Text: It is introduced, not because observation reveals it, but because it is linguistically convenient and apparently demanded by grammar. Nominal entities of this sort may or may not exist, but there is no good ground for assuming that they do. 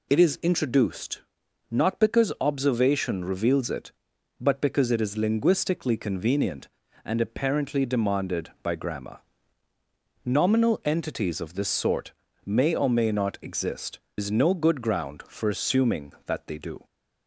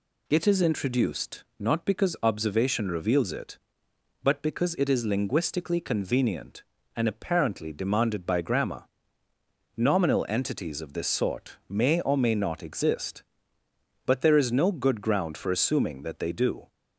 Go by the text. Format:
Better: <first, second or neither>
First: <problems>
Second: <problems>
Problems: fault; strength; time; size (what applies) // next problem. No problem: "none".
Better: second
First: pauses between "sort" and "may"; slight; at 12.1 s; 0.34 s long // skips "but there"; at 14.0 s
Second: none